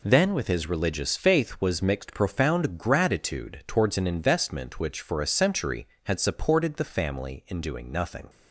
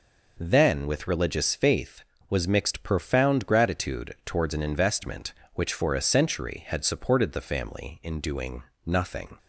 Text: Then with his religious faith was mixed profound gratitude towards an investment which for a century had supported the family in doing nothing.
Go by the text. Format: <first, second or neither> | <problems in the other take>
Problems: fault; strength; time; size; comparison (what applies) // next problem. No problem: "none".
first | skips "his"; at 1.0 s // pauses between "doing" and "nothing"; slight; at 8.6 s; 0.24 s long